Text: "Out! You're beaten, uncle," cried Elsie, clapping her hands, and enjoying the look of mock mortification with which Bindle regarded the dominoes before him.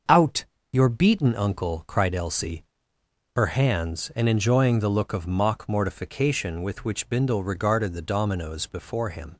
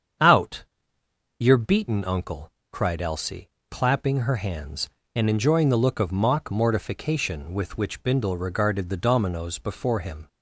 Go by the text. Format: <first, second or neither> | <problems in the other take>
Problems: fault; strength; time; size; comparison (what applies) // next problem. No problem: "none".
second | starts louder than the rest; until 1.3 s; 6.5 dB; strong in the second // skips "clapping"; at 2.9 s